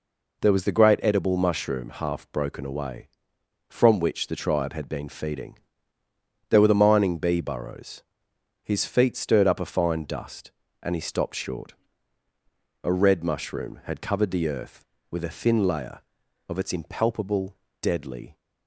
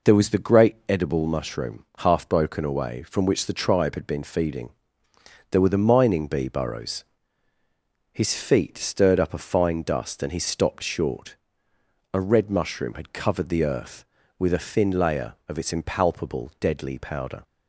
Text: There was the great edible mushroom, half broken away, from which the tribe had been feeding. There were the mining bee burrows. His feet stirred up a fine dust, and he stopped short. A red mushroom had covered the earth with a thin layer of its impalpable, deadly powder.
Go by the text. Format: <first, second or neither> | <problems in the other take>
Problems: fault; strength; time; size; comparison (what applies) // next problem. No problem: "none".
second | stops before "powder"; at 18.3 s